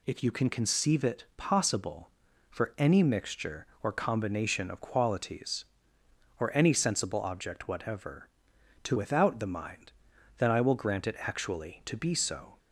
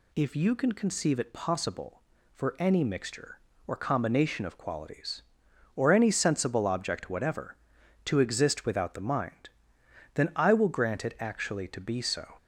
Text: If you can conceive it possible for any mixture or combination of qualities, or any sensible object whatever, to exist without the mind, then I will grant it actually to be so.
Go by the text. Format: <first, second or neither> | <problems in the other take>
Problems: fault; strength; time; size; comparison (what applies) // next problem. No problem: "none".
second | skips "exist"; at 8.9 s